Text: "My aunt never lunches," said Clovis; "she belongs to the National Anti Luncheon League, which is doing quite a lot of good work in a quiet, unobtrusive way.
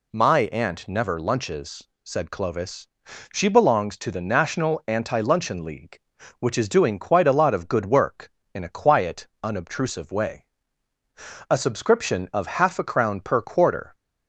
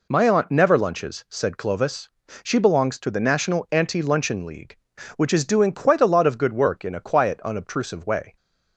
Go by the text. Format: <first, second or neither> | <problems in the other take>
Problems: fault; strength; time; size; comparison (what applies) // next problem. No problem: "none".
second | goes on to say "A subscription of half a crown per quarter"; strong; from 11.4 s on; 2.4 s long